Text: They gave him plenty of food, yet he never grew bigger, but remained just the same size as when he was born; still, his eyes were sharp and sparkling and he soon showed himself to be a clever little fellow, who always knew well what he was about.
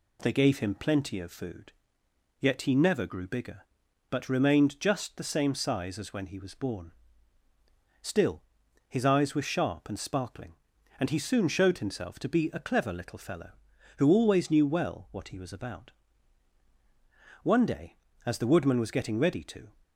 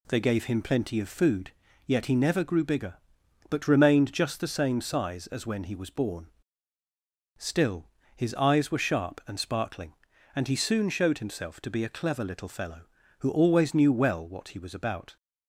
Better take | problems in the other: second | goes on to say "One day as the woodman was getting ready to"; strong; from 17.4 s on; 2.2 s long

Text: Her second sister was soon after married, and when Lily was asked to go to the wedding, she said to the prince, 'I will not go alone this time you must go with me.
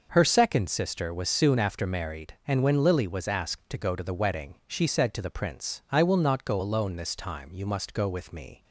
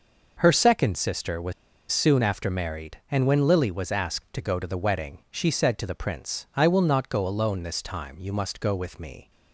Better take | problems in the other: first | pauses between "was" and "soon"; at 1.5 s; 0.39 s long

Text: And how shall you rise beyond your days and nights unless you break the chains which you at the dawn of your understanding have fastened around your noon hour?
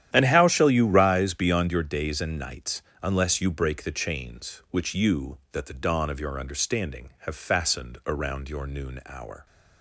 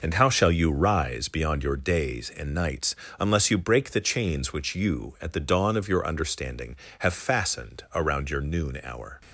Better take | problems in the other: second | starts louder than the rest; strong; until 1.1 s; 11 dB // pauses between "nights" and "unless"; slight; at 2.8 s; 0.20 s long; slight in the second // says "that" for "at"; at 5.5 s

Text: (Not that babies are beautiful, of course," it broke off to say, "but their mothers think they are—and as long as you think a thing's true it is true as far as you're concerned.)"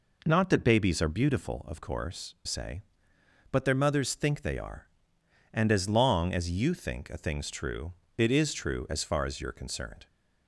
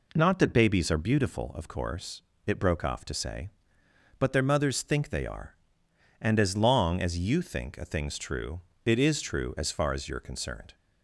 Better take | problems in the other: second | skips "it broke off to"; at 2.4 s // pauses between "true" and "it"; slight; at 7.9 s; 0.24 s long; slight in the second

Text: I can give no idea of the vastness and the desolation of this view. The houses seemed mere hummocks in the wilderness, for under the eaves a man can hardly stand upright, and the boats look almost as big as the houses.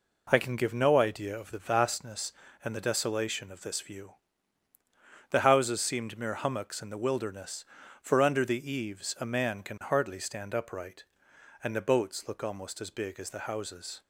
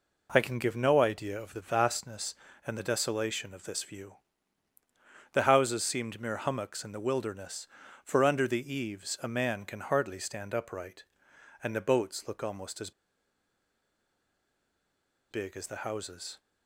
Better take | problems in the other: first | pauses between "as" and "big"; strong; at 12.9 s; 2.3 s long

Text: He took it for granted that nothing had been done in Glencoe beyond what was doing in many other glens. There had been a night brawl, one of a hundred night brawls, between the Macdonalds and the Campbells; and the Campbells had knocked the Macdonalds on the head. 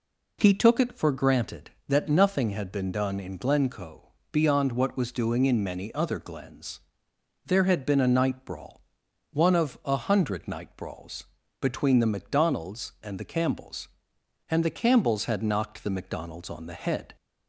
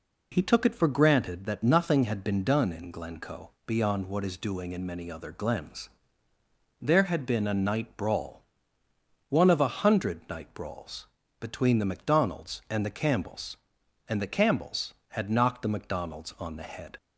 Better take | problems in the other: first | pauses between "Glencoe" and "beyond"; slight; at 3.5 s; 0.16 s long; slight in the first // says "is" for "was"; at 4.2 s

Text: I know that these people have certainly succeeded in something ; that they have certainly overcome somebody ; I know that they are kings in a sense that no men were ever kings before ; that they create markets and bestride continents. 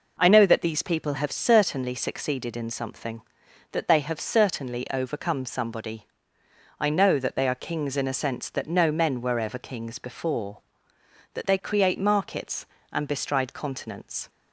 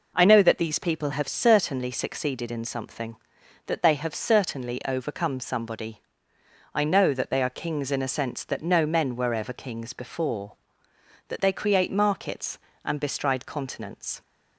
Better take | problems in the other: neither | none

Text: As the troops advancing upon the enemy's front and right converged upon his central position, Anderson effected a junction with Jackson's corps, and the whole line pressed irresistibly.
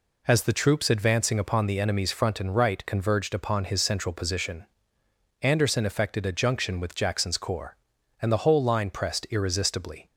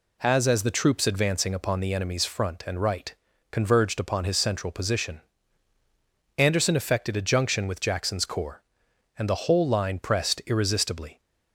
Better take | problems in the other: first | says "As" twice; at 0.4 s // pauses between "right" and "converged"; at 3.1 s; 0.38 s long

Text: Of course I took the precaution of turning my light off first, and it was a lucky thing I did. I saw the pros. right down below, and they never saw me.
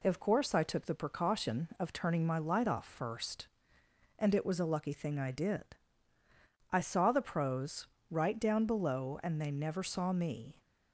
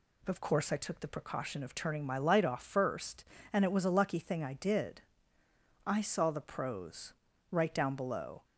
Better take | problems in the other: first | stops before "and they never saw me"; at 8.4 s

